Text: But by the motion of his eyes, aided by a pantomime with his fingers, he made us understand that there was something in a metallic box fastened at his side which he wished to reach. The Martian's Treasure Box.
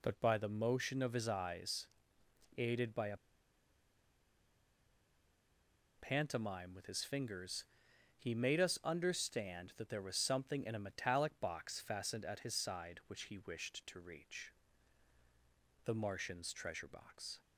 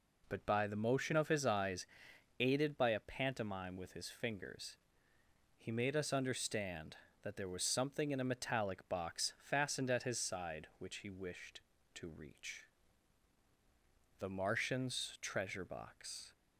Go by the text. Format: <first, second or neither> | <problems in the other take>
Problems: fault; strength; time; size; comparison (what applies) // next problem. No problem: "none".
second | pauses between "a" and "pantomime"; strong; at 3.1 s; 2.8 s long